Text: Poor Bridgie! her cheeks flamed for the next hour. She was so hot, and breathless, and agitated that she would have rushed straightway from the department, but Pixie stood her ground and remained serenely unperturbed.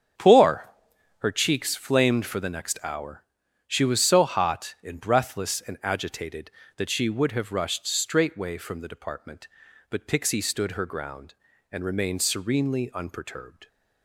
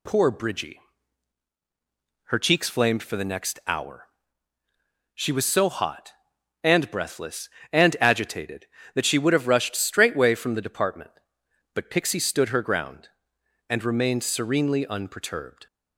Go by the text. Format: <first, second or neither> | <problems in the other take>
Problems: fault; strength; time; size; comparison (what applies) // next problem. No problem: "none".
second | starts louder than the rest; strong; until 1.6 s; 8 dB // skips "Bridgie"; at 0.9 s